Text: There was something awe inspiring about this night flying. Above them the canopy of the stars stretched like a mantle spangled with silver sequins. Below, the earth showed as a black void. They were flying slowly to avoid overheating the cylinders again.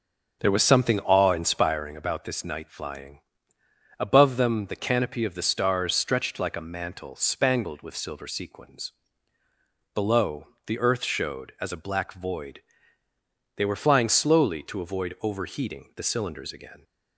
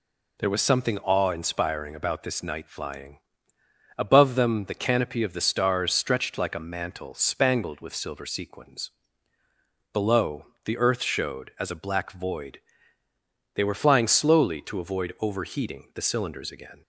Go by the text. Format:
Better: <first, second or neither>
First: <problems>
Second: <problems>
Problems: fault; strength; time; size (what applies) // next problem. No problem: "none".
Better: second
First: starts louder than the rest; until 1.9 s; 6.5 dB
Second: none